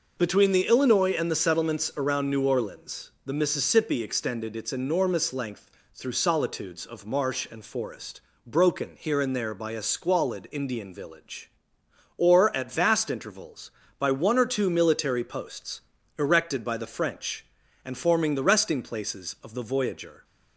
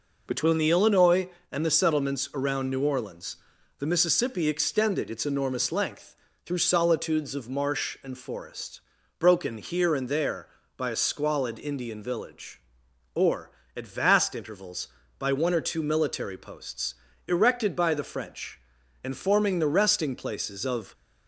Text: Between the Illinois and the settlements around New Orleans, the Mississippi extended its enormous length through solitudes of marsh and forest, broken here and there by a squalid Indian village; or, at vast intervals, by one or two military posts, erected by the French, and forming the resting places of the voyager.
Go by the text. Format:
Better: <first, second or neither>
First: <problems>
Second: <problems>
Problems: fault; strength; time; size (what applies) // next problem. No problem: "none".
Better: first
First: pauses between "length" and "through"; slight; at 5.6 s; 0.24 s long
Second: pauses between "length" and "through"; slight; at 6.1 s; 0.30 s long // stops before "the voyager"; at 20.9 s